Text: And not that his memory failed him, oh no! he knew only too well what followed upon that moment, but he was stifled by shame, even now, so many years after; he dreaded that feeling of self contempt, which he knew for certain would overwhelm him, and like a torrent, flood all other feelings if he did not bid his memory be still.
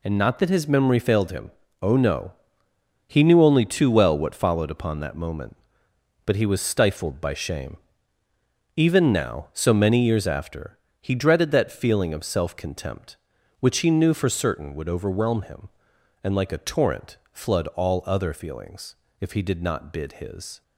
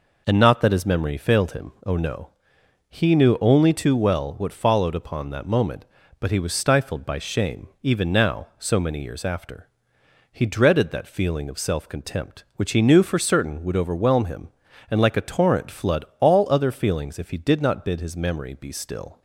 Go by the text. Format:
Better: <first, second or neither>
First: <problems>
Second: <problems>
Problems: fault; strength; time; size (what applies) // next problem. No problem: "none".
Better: second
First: pauses between "feelings" and "if"; slight; at 18.9 s; 0.24 s long // stops before "memory be still"; at 20.6 s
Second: none